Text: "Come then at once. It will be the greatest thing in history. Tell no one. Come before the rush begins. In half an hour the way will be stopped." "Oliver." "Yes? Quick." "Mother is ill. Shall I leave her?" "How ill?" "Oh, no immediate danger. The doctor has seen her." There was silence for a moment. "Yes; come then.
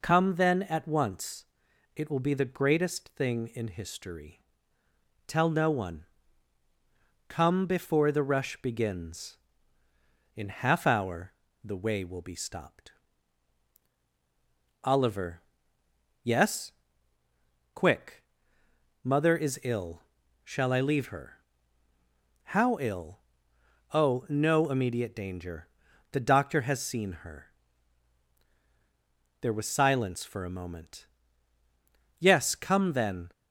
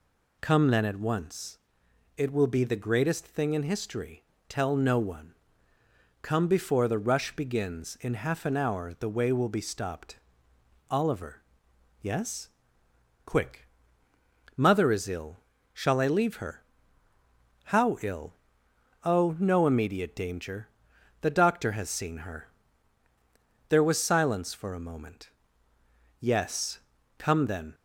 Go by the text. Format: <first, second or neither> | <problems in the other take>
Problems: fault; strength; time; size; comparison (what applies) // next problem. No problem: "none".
second | skips "an"; at 10.8 s // pauses between "hour" and "the"; slight; at 11.3 s; 0.32 s long